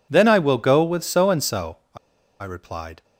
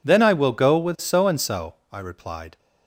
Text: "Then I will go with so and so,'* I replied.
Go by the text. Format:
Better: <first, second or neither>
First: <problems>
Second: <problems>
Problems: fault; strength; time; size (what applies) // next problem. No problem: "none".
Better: second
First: pauses between "I" and "replied"; at 1.9 s; 0.44 s long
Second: none